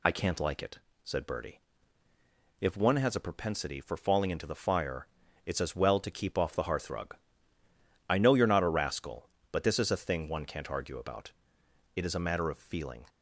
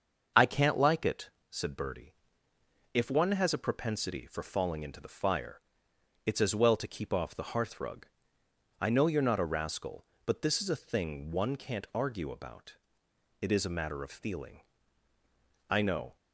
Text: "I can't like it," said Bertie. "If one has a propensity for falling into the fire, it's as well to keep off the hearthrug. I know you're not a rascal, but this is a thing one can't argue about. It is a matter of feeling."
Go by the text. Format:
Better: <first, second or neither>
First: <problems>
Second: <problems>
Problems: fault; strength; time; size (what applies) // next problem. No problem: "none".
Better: first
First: none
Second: starts louder than the rest; until 1.5 s; 6.5 dB // goes on to say "I know"; slight; from 15.6 s on; 0.46 s long